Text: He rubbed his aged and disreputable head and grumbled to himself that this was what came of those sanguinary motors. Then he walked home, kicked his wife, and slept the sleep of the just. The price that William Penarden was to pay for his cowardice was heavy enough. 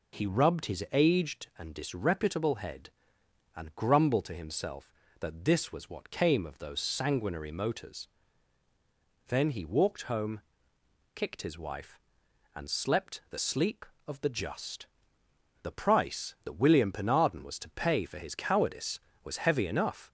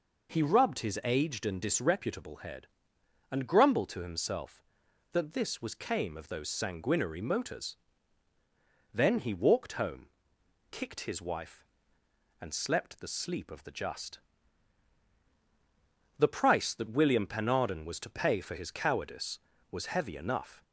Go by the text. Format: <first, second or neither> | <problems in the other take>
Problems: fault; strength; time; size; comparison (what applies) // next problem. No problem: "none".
first | skips "what"; at 5.7 s